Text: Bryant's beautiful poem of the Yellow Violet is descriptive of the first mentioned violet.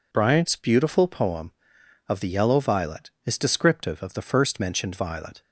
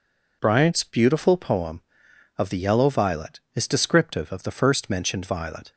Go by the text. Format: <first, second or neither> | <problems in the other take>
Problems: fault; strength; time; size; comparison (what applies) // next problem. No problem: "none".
neither | none